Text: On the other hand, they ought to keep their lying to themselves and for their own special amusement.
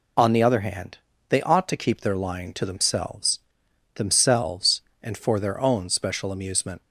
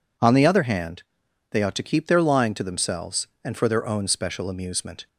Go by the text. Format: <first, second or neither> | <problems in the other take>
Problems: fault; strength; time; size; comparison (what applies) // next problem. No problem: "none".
second | says "themselves" twice; at 3.9 s